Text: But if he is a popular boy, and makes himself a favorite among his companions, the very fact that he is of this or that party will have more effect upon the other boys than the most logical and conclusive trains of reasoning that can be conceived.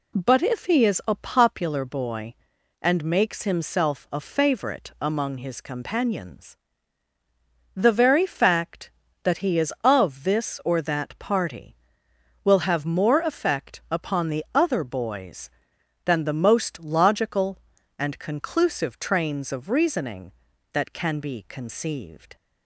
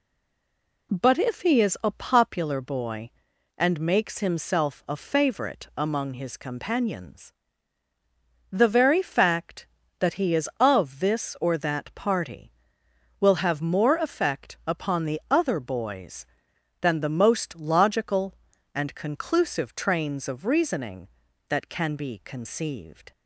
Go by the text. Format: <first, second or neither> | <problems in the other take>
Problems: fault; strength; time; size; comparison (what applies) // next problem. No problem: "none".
first | stays silent before the first word; slight; until 0.9 s; 0.9 s long